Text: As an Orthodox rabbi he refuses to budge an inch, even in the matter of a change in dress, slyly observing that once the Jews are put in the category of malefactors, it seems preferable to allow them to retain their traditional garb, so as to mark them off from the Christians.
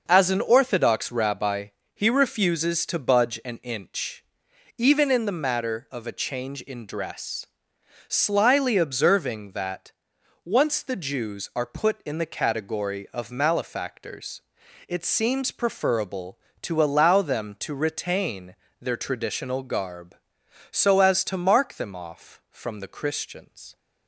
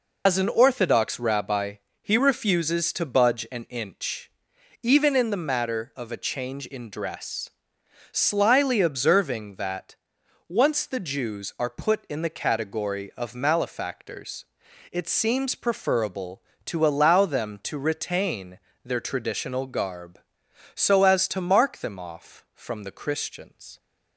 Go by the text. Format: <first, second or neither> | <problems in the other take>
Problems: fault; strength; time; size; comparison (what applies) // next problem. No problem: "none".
first | loses the start of "As"; at 0.2 s; 95 ms // pauses between "rabbi" and "he"; slight; at 1.7 s; 0.26 s long; slight in the first // pauses between "that" and "once"; noticeable; at 9.9 s; 0.54 s long; noticeable in the first // pauses between "retain" and "their"; slight; at 18.5 s; 0.26 s long; slight in the first